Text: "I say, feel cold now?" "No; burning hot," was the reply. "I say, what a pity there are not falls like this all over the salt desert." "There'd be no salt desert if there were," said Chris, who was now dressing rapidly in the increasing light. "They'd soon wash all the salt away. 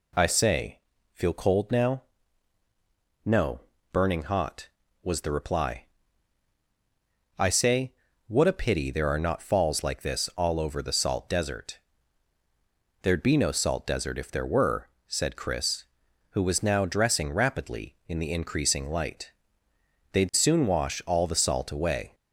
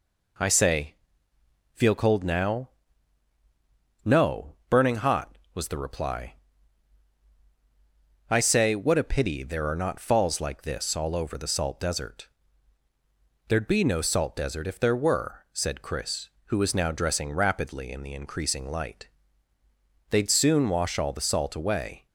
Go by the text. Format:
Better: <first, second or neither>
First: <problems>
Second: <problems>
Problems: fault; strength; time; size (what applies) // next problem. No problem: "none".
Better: neither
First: none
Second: none